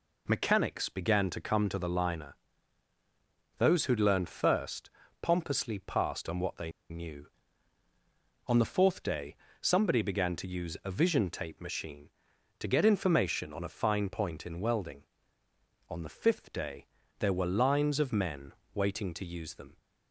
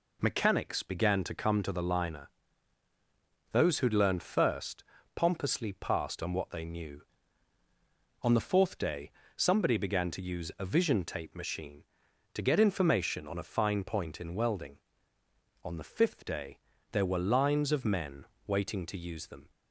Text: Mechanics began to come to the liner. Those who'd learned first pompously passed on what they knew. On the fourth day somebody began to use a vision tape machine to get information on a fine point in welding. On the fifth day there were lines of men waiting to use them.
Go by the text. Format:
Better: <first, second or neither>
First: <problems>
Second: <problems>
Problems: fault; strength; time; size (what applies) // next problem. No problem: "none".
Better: second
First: pauses between "first" and "pompously"; slight; at 4.9 s; 0.30 s long // pauses between "they" and "knew"; slight; at 6.6 s; 0.21 s long // pauses between "day" and "somebody"; slight; at 9.3 s; 0.24 s long // pauses between "day" and "there"; slight; at 16.8 s; 0.34 s long // pauses between "men" and "waiting"; slight; at 18.5 s; 0.24 s long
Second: pauses between "first" and "pompously"; slight; at 4.8 s; 0.30 s long // pauses between "day" and "somebody"; slight; at 9.1 s; 0.24 s long // pauses between "day" and "there"; slight; at 16.5 s; 0.34 s long // pauses between "men" and "waiting"; slight; at 18.2 s; 0.24 s long